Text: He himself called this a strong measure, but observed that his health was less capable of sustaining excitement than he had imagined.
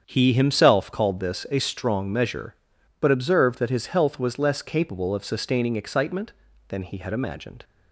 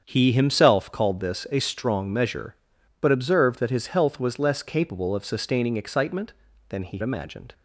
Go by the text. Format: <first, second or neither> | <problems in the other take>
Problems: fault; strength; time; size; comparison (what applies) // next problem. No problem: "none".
first | starts louder than the rest; strong; until 1.0 s; 7.5 dB; strong in the first // skips "had"; at 7.0 s